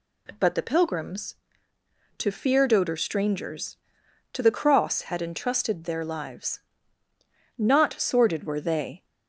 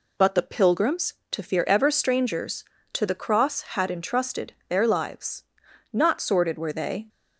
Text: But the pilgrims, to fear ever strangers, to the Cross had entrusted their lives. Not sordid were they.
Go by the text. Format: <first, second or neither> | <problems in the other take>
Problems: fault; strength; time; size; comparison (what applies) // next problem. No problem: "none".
second | says "doder" for "ever"; at 2.6 s